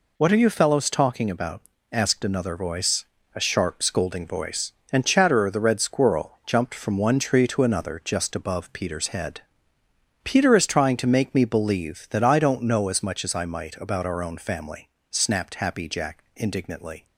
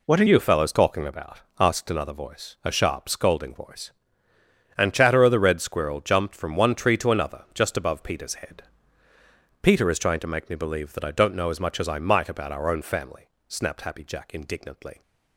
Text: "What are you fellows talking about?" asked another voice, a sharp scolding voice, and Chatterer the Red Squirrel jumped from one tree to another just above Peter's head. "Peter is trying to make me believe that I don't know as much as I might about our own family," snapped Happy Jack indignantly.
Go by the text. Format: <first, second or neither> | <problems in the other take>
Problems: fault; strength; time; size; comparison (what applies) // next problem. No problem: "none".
first | changes voice at "you"; from 0.2 s on; 14.8 s long